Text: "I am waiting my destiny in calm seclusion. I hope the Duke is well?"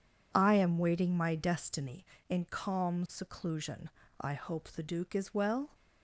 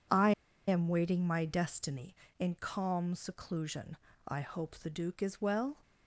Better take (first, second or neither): first